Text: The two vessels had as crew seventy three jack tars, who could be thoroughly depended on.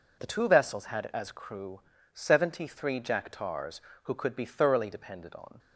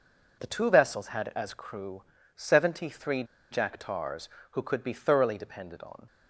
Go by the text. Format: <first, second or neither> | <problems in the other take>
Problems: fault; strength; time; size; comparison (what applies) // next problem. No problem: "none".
first | pauses between "crew" and "seventy"; slight; at 2.0 s; 0.32 s long; slight in the first // pauses between "three" and "jack"; slight; at 3.2 s; 0.26 s long